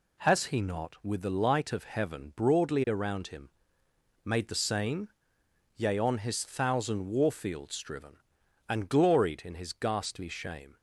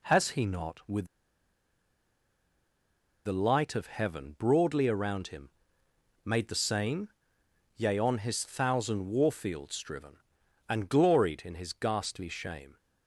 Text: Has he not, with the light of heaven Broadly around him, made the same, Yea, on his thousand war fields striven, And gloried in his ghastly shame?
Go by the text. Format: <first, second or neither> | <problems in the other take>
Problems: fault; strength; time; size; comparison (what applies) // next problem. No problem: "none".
first | pauses between "with" and "the"; strong; at 1.0 s; 2.2 s long